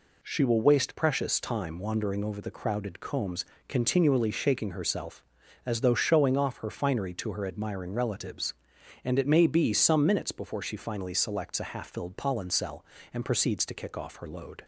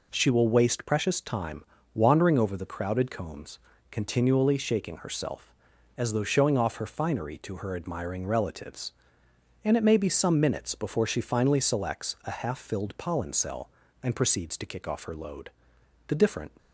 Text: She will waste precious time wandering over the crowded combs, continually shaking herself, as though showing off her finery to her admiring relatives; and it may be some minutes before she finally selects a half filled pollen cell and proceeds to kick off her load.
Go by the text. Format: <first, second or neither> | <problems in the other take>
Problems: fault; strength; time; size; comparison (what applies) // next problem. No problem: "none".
first | pauses between "time" and "wandering"; slight; at 1.6 s; 0.30 s long // goes on to say "The different"; slight; from 16.0 s on; 0.42 s long